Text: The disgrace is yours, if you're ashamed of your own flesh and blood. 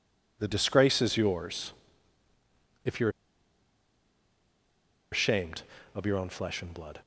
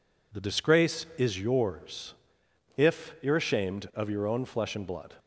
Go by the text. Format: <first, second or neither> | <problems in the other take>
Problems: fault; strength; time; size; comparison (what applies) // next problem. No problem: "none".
second | pauses between "you're" and "ashamed"; strong; at 3.0 s; 2.0 s long